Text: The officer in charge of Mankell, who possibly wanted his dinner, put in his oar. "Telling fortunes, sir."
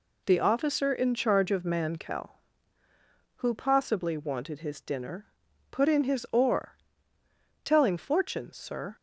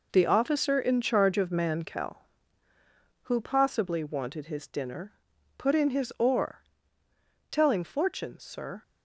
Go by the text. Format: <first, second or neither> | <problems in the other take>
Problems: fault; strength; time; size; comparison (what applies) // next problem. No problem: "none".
first | gets quieter; strong; throughout; 9.5 dB